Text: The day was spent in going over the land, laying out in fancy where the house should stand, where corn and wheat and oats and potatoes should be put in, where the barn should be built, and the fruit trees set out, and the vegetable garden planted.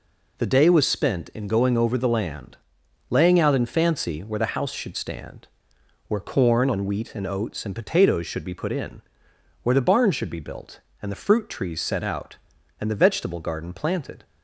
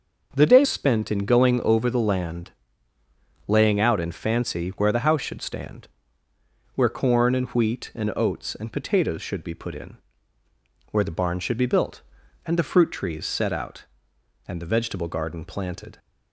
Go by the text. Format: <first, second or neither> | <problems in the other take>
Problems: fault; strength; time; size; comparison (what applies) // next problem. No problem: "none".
first | starts louder than the rest; until 1.3 s; 6 dB // skips "was"; at 0.6 s